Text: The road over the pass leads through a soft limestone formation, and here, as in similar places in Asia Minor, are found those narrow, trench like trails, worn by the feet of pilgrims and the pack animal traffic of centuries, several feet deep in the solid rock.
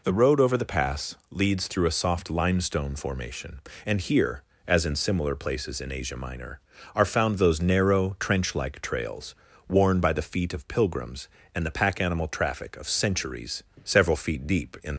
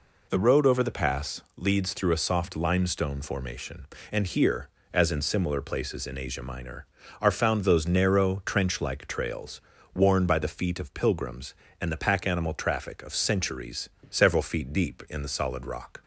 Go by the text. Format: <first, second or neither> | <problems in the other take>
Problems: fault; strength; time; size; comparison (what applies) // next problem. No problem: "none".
second | pauses between "pass" and "leads"; slight; at 1.1 s; 0.16 s long; slight in the second // stops before "the solid rock"; at 14.9 s